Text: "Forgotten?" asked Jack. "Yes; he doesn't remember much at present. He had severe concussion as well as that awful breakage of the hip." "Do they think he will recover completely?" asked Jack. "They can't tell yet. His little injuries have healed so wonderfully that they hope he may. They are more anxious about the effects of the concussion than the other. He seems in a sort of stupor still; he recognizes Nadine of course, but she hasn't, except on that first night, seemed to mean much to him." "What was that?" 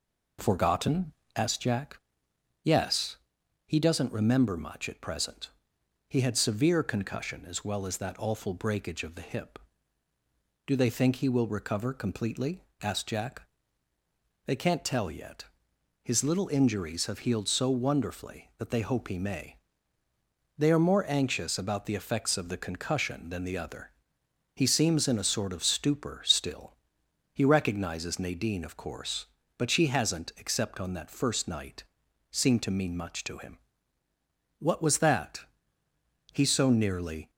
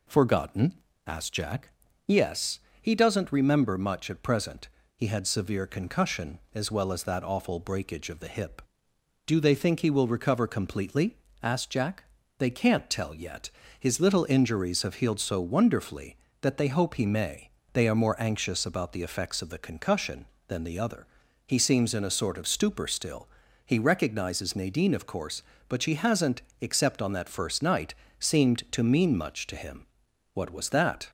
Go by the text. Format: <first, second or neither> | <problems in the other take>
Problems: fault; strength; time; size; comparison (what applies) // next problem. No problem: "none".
second | goes on to say "He so nearly"; noticeable; from 36.3 s on; 0.96 s long